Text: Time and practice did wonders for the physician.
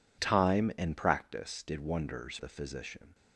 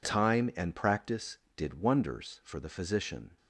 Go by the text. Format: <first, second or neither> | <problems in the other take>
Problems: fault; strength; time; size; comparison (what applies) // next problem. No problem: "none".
second | skips "for"; at 2.3 s